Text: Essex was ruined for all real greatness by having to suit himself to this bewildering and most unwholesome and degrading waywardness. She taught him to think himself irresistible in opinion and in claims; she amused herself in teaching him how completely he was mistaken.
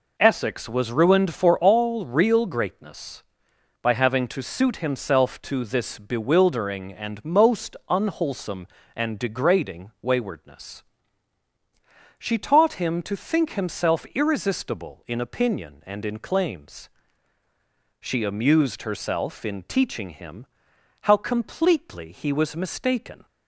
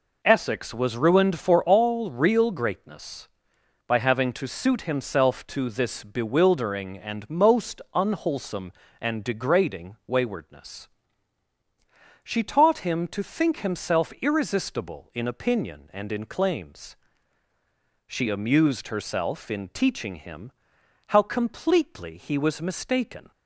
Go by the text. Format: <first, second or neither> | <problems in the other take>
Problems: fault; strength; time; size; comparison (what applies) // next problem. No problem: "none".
neither | pauses between "him" and "how"; noticeable; the same in both